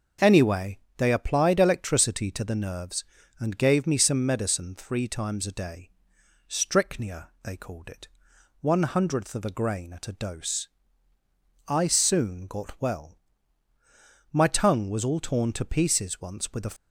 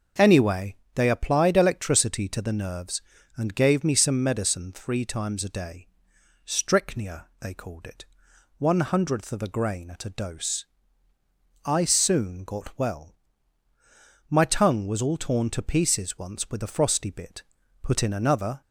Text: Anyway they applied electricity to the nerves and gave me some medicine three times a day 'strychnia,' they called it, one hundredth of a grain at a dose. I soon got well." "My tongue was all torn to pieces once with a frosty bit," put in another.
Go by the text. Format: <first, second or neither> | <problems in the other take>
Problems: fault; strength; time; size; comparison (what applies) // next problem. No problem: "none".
second | starts louder than the rest; until 1.4 s; 6.5 dB; also in the second // pauses between "Anyway" and "they"; slight; at 0.7 s; 0.20 s long; slight in the second // pauses between "day" and "strychnia"; noticeable; at 5.8 s; 0.62 s long; noticeable in the second // stops before "frosty bit put in another"; at 16.7 s